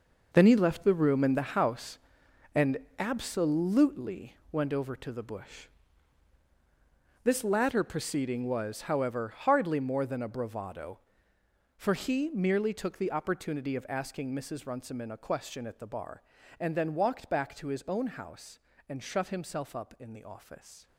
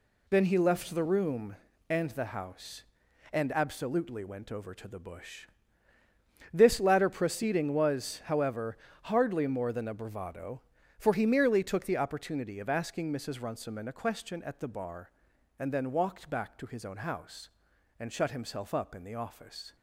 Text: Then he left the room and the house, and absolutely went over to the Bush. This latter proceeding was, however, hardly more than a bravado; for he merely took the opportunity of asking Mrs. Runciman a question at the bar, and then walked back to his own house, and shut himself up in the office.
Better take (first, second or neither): second